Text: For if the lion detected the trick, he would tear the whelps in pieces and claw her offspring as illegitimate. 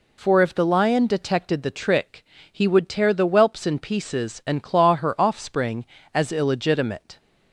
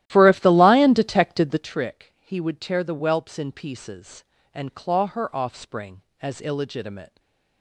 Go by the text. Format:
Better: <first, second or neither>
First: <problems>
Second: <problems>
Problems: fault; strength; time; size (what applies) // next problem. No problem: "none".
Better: first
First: none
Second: starts louder than the rest; strong; until 1.8 s; 14 dB // stays silent after the last word; slight; from 7.0 s on; 0.6 s long